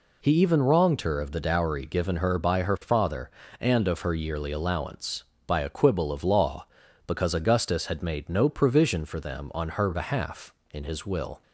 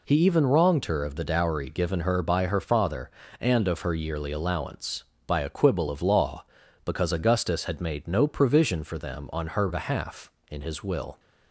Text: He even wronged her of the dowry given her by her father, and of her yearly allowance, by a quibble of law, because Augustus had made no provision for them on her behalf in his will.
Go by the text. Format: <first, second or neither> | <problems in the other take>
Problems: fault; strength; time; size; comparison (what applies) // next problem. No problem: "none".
neither | none